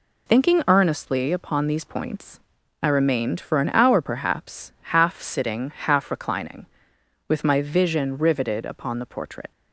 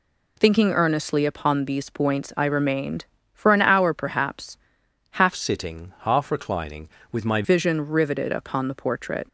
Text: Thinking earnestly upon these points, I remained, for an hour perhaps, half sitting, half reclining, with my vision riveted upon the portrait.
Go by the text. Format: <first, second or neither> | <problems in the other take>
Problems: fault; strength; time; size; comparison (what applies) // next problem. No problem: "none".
first | changes voice from "sitting" to "my"; from 5.3 to 7.4 s; 2.1 s long